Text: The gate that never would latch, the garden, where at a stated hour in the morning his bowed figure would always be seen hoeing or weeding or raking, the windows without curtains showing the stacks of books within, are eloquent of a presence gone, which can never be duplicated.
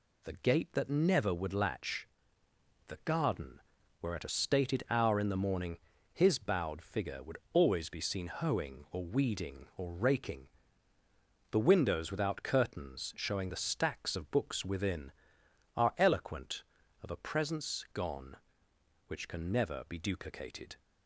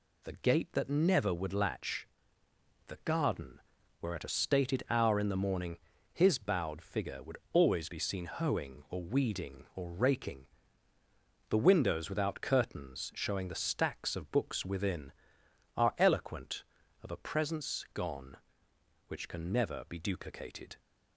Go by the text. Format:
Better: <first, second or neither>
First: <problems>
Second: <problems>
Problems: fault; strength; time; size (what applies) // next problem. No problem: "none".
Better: neither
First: pauses between "morning" and "his"; slight; at 5.7 s; 0.34 s long // pauses between "would" and "always"; slight; at 7.3 s; 0.16 s long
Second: pauses between "morning" and "his"; slight; at 5.7 s; 0.34 s long // pauses between "would" and "always"; slight; at 7.3 s; 0.16 s long